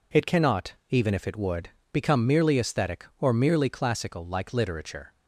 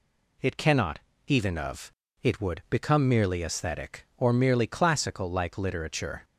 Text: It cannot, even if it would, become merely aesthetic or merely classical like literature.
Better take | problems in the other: first | says "of" for "if"; at 1.5 s

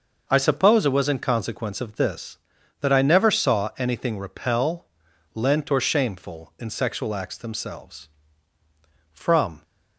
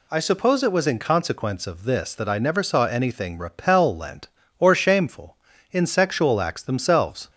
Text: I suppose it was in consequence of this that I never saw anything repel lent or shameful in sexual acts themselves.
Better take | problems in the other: second | pauses between "repel" and "lent"; noticeable; at 4.8 s; 0.50 s long // goes on to say "From"; from 9.1 s on; 0.52 s long

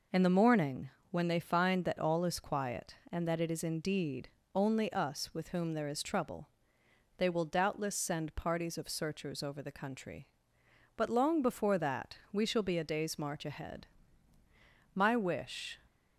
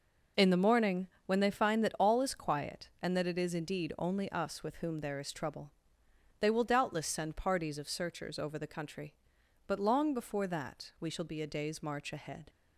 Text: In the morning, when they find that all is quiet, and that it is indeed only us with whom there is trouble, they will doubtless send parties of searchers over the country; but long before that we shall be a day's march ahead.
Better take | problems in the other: second | pauses between "indeed" and "only"; slight; at 4.2 s; 0.26 s long // goes on to say "My wish"; noticeable; from 14.9 s on; 0.84 s long

